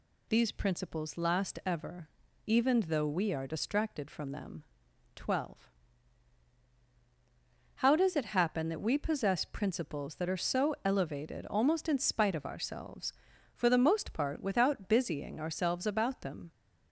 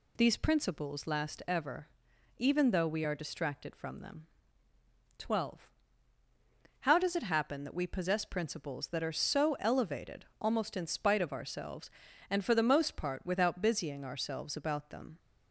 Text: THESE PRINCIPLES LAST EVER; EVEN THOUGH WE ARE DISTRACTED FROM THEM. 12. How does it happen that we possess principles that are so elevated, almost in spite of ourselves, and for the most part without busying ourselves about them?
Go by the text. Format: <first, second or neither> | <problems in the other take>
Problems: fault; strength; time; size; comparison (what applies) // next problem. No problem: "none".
second | skips "and"; at 13.3 s